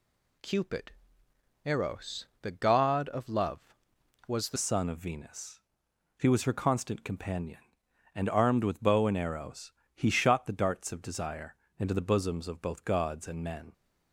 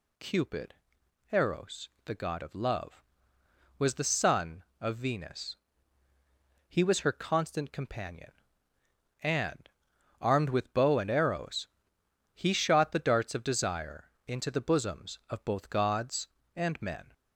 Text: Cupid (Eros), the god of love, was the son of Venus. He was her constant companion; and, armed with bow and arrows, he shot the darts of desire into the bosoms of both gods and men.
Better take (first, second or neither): second